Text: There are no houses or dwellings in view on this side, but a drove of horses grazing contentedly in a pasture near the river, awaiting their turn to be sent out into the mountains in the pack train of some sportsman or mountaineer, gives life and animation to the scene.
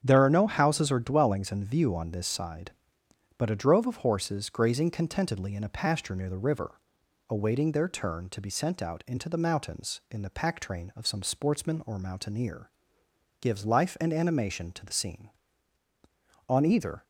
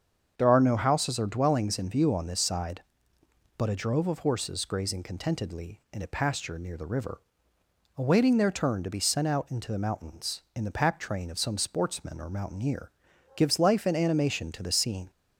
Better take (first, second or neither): second